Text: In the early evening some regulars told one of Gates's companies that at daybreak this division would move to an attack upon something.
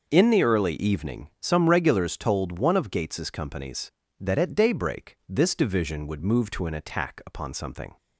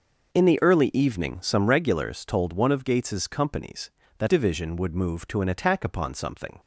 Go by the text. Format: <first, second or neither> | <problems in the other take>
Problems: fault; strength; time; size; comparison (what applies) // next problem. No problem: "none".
first | skips "at daybreak this"; at 4.2 s